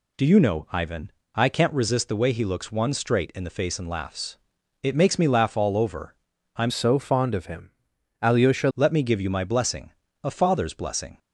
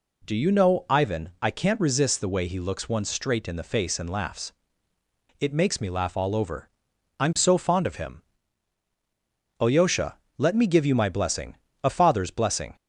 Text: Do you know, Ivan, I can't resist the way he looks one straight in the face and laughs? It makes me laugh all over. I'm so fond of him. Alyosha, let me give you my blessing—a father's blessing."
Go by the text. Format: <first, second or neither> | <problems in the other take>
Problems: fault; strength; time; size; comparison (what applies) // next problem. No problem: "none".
second | changes voice from "so" to "Alyosha"; from 6.6 to 8.6 s; 2.0 s long